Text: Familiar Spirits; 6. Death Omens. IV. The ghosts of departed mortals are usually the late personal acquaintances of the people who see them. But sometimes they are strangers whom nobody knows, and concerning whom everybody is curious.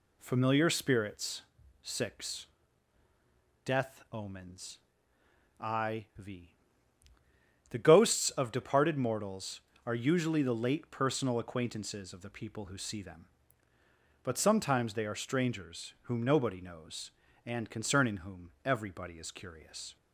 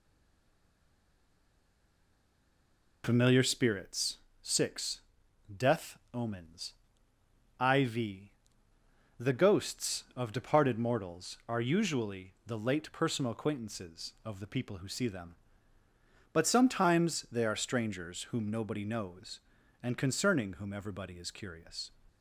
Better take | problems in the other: first | stays silent before the first word; strong; until 3.0 s; 3.0 s long

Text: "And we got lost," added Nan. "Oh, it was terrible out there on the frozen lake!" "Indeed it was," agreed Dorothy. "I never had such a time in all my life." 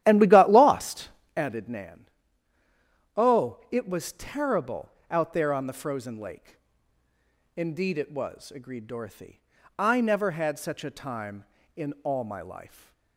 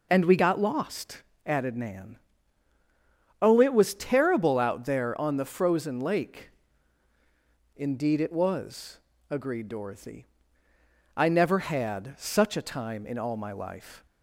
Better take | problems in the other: second | starts louder than the rest; strong; until 1.4 s; 12.5 dB // pauses between "terrible" and "out"; slight; at 4.8 s; 0.20 s long

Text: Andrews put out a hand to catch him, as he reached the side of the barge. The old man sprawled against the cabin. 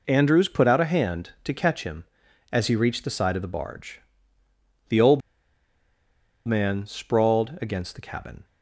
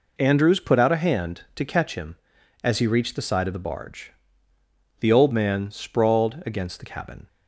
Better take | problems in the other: second | pauses between "old" and "man"; strong; at 5.2 s; 1.2 s long

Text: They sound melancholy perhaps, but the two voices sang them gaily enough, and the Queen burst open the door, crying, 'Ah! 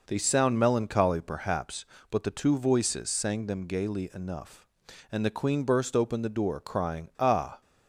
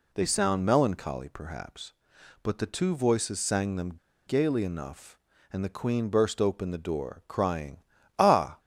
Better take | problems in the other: first | pauses between "them" and "gaily"; slight; at 3.9 s; 0.30 s long

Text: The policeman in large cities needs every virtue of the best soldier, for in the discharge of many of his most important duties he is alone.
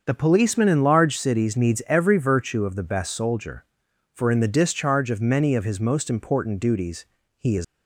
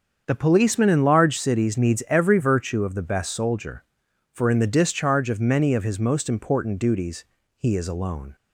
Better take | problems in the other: second | starts louder than the rest; until 1.0 s; 6.5 dB; also in the second // pauses between "duties" and "he"; slight; at 7.0 s; 0.32 s long; slight in the second // stops before "alone"; at 7.6 s

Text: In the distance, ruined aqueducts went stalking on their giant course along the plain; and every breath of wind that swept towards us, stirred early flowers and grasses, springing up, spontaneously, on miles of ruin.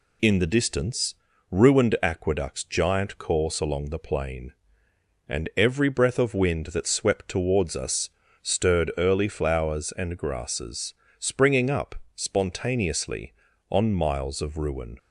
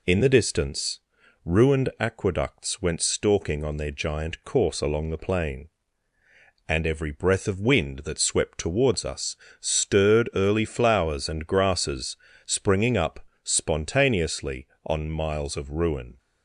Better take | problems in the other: second | skips "went stalking on their"; at 2.6 s

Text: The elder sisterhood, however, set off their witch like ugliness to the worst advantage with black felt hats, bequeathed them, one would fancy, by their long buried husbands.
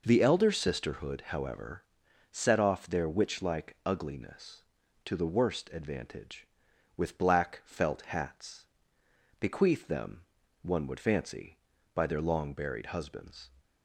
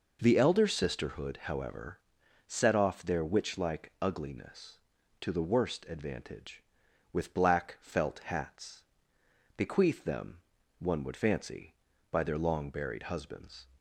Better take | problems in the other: neither | none

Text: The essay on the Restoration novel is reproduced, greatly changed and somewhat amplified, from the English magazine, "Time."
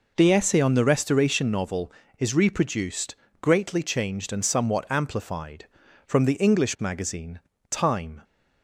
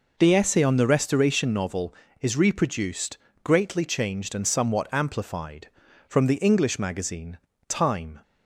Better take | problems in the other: neither | none

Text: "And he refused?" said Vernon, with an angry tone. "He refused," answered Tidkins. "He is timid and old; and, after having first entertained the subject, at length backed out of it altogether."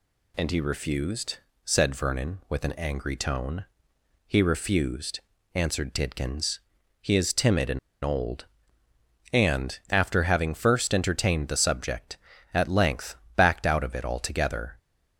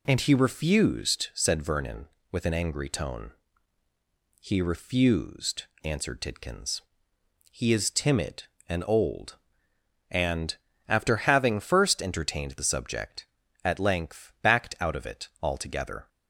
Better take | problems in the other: second | pauses between "and" and "old"; slight; at 7.7 s; 0.25 s long // pauses between "length" and "backed"; slight; at 13.1 s; 0.22 s long

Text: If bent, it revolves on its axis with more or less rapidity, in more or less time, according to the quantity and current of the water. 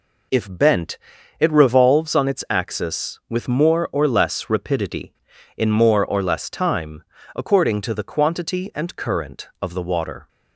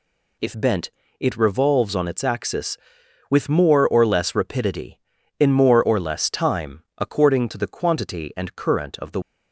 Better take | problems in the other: first | stops before "water"; at 9.2 s

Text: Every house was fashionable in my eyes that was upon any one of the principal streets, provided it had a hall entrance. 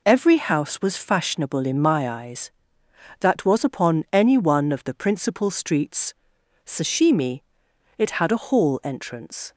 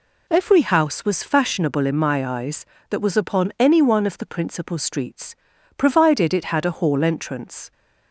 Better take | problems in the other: second | says "sashimi" for "provided"; at 6.6 s

